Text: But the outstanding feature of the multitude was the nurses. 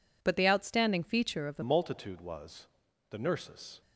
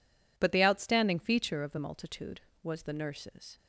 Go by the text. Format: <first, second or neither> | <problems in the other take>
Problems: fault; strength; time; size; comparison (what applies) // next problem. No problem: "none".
second | changes voice at "multitude"; from 1.6 s on; 2.2 s long // pauses between "was" and "the"; at 2.6 s; 0.42 s long